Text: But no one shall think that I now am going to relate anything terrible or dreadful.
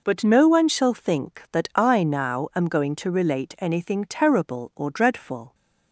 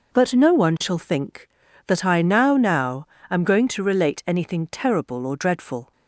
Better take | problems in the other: first | says "now" twice; at 2.5 s

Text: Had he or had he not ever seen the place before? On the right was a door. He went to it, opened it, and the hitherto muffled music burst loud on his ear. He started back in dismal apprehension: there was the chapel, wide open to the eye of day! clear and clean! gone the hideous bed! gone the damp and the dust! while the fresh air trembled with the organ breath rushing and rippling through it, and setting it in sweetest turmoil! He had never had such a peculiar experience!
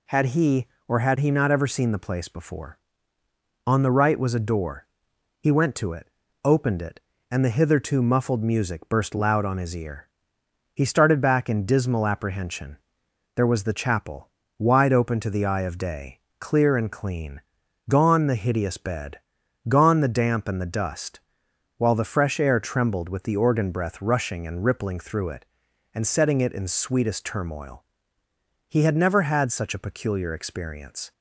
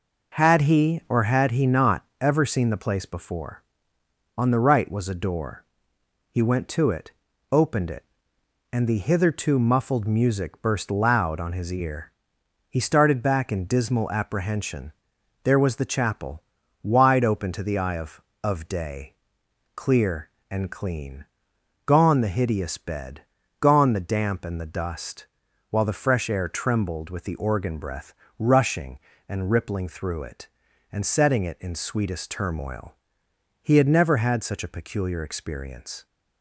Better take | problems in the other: first | says "of" twice; at 18.4 s // pauses between "breath" and "rushing"; slight; at 28.1 s; 0.26 s long

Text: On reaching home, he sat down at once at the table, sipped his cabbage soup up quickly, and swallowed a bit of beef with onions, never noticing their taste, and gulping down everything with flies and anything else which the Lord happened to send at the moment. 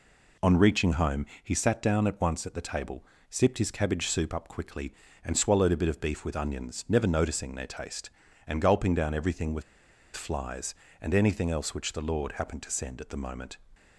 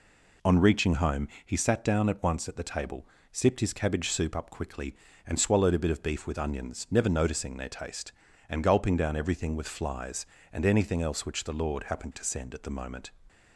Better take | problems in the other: second | pauses between "with" and "flies"; noticeable; at 9.6 s; 0.53 s long

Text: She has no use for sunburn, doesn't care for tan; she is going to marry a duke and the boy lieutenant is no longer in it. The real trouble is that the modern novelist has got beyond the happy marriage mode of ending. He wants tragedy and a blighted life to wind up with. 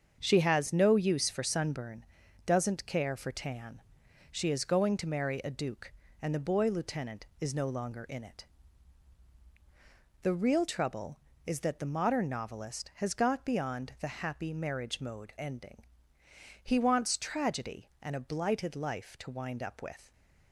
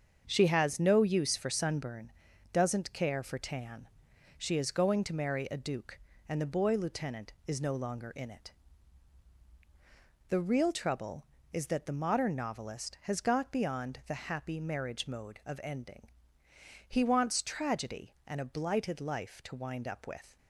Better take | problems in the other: second | starts louder than the rest; until 1.2 s; 7 dB; also in the second // skips "of"; at 15.3 s // stays silent after the last word; slight; from 20.0 s on; 0.5 s long

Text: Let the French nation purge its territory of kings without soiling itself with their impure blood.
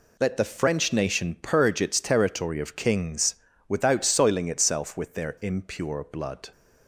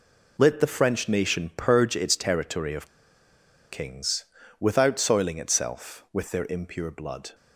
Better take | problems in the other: first | pauses between "of" and "kings"; noticeable; at 2.8 s; 0.84 s long // pauses between "kings" and "without"; slight; at 4.2 s; 0.34 s long; slight in the first

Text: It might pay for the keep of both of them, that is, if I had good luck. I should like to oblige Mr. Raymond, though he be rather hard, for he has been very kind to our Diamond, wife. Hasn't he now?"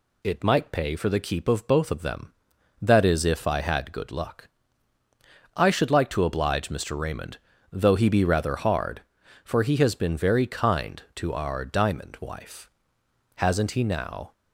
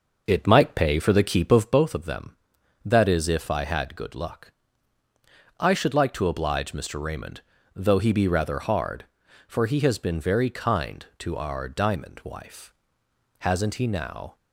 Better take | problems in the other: first | starts louder than the rest; noticeable; until 1.9 s; 6 dB

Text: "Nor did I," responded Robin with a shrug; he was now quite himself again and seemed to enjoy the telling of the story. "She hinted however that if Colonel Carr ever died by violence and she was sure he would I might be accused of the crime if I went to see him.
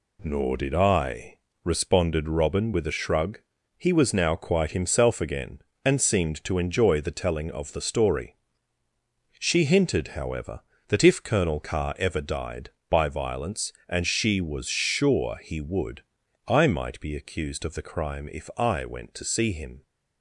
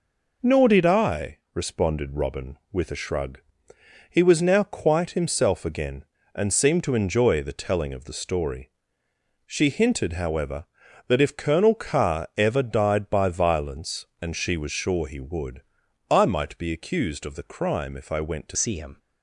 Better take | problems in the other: first | pauses between "would" and "I"; at 15.6 s; 0.44 s long; noticeable in the first // changes voice at "see"; from 18.5 s on; 0.4 s long

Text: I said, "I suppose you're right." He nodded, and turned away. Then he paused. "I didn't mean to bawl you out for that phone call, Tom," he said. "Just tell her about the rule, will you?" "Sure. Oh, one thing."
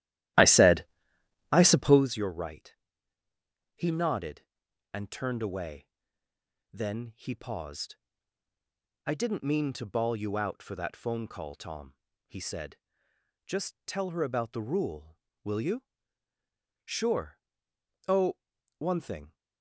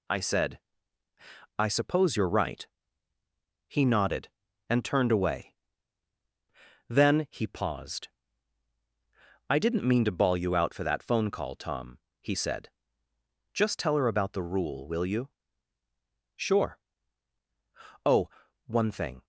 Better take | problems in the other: second | starts louder than the rest; strong; until 2.2 s; 14.5 dB

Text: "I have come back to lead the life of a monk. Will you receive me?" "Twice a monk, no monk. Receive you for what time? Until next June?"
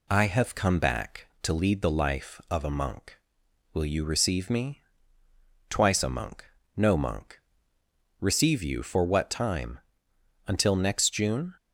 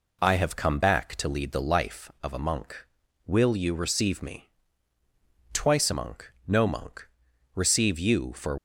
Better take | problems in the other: first | stops before "what time Until next June"; at 8.5 s

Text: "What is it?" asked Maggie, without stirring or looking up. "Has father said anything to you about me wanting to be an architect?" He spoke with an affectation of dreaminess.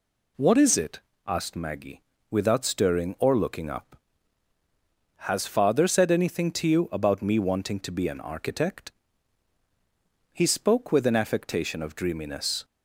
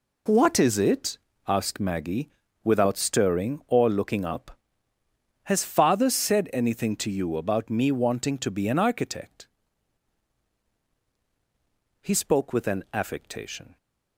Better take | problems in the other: first | stops before "of dreaminess"; at 13.7 s

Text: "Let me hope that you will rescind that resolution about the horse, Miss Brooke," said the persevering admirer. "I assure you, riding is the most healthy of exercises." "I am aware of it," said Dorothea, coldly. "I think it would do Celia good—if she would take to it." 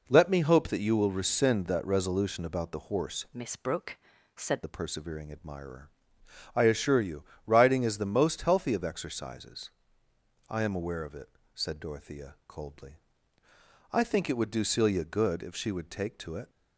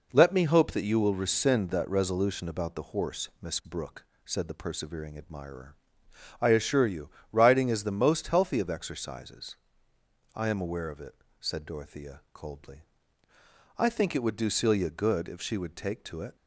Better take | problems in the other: second | changes voice from "Miss" to "said"; from 3.3 to 4.6 s; 1.3 s long

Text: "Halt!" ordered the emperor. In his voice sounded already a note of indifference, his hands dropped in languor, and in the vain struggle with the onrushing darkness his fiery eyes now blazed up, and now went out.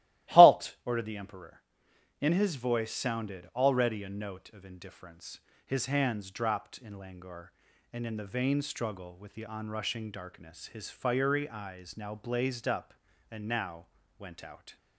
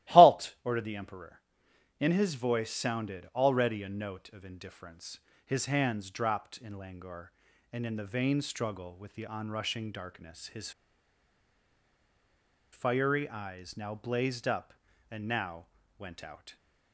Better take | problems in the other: first | starts louder than the rest; strong; until 1.1 s; 15.5 dB; strong in the first // pauses between "his" and "fiery"; strong; at 10.7 s; 2.0 s long // pauses between "now" and "went"; slight; at 15.6 s; 0.32 s long; slight in the first

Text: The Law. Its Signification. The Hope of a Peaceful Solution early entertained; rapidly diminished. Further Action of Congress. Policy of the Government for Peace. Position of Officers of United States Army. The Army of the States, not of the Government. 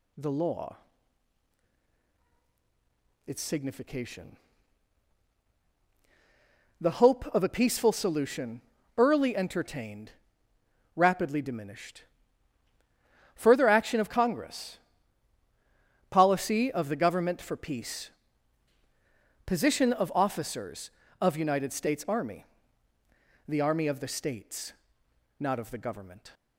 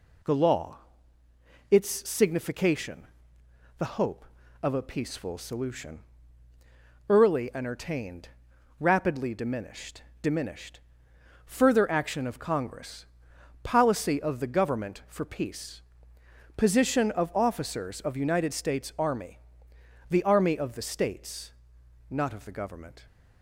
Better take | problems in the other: first | pauses between "Solution" and "early"; at 5.9 s; 1.1 s long; slight in the first // says "diminished" twice; at 10.2 s

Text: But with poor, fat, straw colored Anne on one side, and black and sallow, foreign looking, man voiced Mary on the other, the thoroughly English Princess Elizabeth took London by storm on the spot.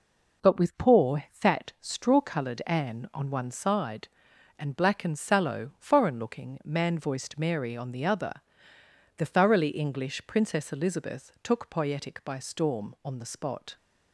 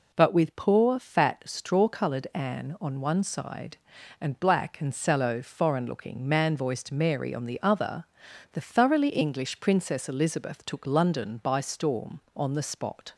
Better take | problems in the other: second | says "Poietic" for "London"; at 11.6 s

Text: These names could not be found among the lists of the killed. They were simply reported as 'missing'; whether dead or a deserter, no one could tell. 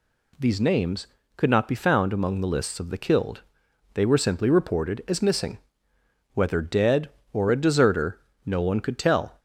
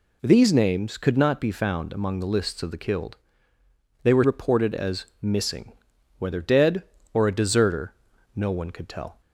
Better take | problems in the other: first | skips "simply"; at 4.2 s // pauses between "as" and "missing"; slight; at 5.0 s; 0.16 s long

